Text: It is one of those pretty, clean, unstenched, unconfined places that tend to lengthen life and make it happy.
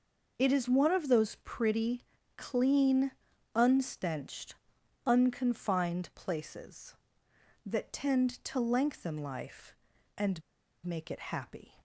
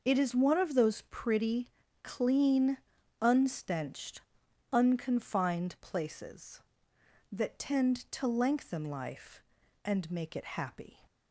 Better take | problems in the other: second | pauses between "and" and "make"; at 10.4 s; 0.43 s long

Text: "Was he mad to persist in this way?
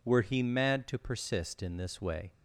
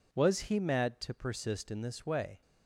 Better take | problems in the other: second | says "Were" for "Was"; at 0.0 s

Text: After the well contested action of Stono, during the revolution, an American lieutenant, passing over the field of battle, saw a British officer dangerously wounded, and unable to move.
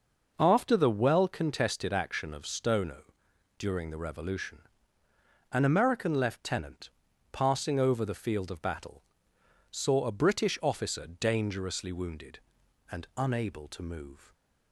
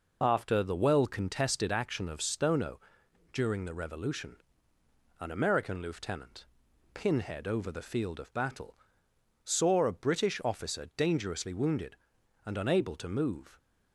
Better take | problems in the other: first | says "pinhead" for "passing"; at 6.9 s

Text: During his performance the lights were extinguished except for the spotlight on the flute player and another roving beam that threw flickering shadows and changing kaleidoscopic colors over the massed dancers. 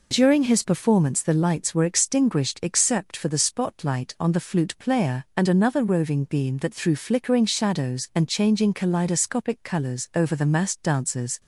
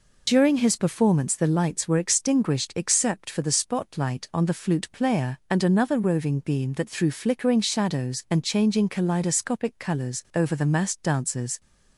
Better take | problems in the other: first | loses the start of "During"; at 0.2 s; 30 ms

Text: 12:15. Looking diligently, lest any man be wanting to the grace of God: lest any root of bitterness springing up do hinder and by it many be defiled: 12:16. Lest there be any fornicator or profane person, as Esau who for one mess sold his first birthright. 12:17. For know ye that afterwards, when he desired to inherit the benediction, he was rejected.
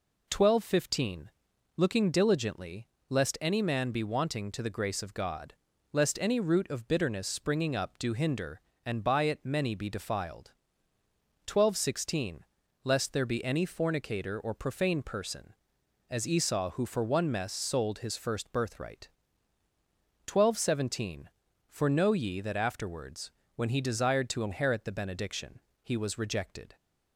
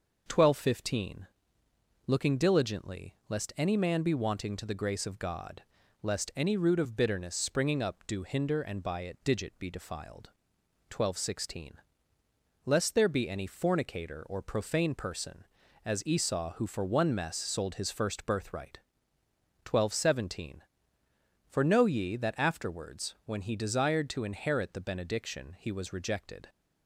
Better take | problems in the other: first | says "digit" for "many"; at 9.2 s

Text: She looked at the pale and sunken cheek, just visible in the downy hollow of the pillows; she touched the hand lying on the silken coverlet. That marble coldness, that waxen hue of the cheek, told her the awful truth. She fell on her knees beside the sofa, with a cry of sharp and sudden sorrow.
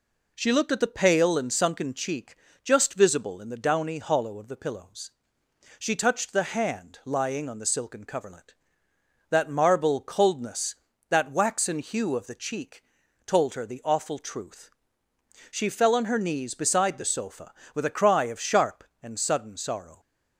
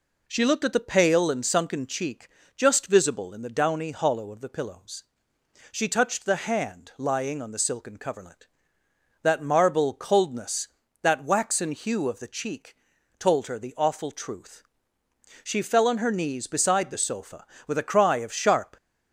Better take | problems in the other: first | stops before "and sudden sorrow"; at 18.7 s

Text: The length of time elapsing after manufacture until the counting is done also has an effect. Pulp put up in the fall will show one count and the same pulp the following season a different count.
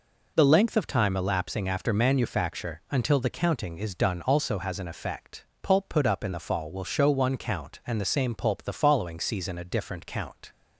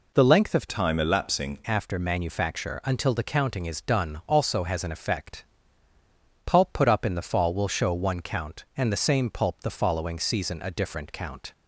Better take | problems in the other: first | changes voice from "time" to "elapsing"; from 0.6 to 1.5 s; 0.9 s long

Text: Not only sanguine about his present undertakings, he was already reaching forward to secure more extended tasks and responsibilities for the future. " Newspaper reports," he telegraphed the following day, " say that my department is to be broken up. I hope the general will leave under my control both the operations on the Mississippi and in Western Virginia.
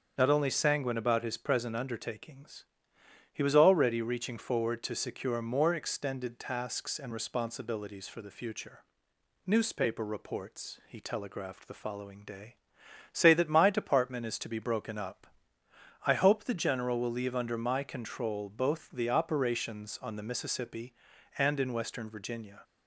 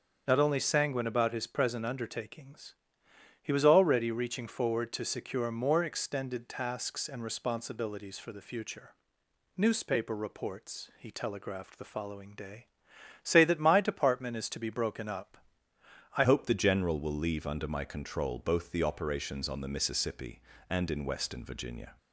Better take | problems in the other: first | starts louder than the rest; strong; until 1.2 s; 7.5 dB; strong in the first // changes voice at "hope"; from 16.2 s on; 5.7 s long

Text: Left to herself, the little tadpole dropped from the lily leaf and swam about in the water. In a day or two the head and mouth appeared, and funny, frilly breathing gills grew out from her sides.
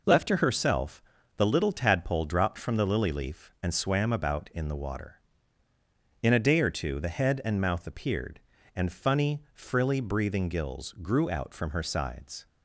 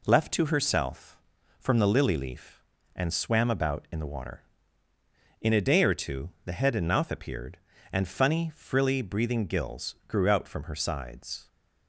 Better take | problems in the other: first | skips "the little tadpole dropped"; at 1.3 s // pauses between "two" and "the"; slight; at 6.2 s; 0.16 s long

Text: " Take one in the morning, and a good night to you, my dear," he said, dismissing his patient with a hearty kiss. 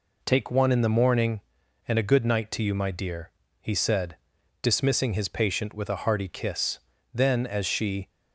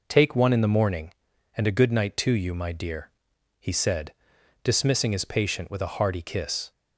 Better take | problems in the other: second | goes on to say "Then as she"; noticeable; from 7.1 s on; 0.96 s long

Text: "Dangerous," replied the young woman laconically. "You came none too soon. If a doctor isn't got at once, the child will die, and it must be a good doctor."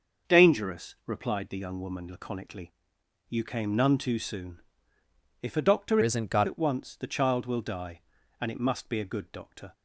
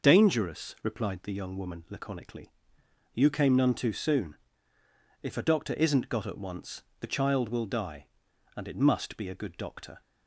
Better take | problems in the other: second | starts louder than the rest; noticeable; until 1.3 s; 6 dB // changes voice from "isn't" to "got"; from 6.0 to 6.4 s; 0.4 s long

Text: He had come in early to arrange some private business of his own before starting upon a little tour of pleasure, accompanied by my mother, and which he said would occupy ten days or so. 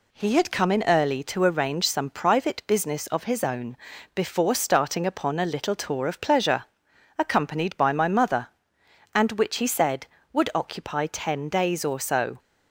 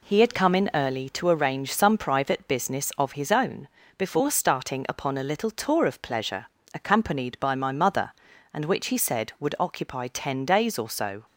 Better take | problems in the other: neither | pauses between "own" and "before"; the same in both

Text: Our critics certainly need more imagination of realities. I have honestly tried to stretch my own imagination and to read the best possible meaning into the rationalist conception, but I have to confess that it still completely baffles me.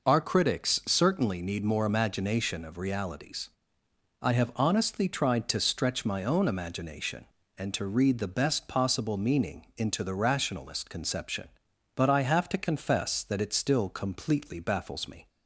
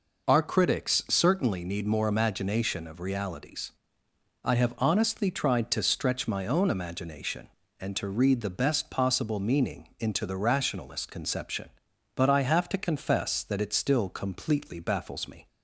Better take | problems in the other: neither | none

